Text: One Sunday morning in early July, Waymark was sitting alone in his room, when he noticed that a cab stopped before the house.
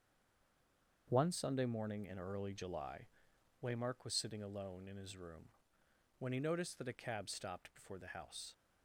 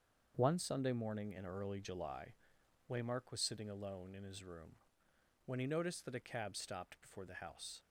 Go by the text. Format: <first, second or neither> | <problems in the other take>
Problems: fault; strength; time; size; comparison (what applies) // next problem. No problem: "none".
second | stays silent before the first word; until 1.0 s; 1.0 s long // starts louder than the rest; until 2.1 s; 7 dB; also in the second